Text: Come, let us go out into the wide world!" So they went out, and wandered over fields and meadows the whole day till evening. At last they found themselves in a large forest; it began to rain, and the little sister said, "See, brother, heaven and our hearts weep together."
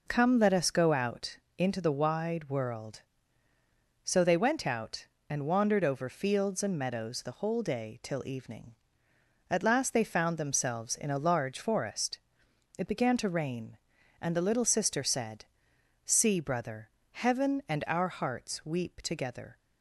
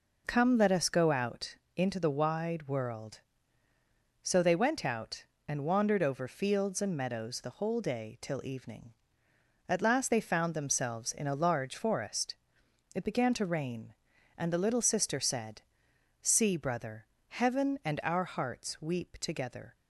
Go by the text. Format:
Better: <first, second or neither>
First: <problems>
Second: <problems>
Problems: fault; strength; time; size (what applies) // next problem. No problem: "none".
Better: neither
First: pauses between "out" and "into"; slight; at 1.3 s; 0.20 s long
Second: pauses between "out" and "into"; slight; at 1.5 s; 0.20 s long